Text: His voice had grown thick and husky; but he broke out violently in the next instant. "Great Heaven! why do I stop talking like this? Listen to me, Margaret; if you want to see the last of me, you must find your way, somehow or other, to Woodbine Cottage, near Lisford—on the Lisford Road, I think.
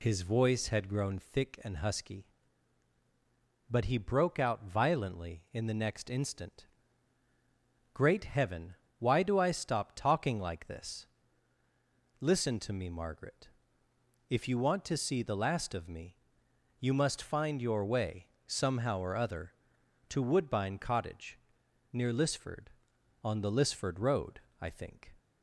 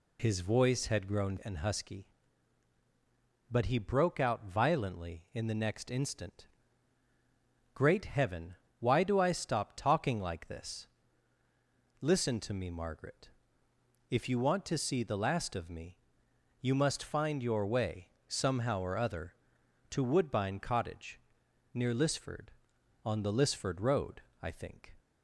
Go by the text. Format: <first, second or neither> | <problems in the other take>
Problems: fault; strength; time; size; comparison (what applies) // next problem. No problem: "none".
first | skips "thick"; at 1.4 s